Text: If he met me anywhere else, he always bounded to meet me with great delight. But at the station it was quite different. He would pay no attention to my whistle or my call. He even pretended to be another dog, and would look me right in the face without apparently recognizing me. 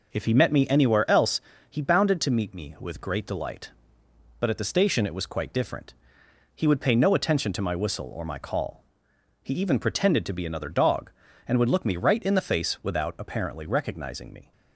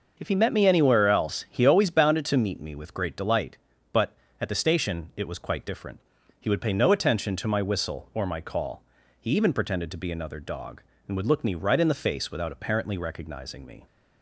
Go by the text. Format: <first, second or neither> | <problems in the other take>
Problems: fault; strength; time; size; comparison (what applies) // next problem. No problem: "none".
second | skips "always"; at 1.8 s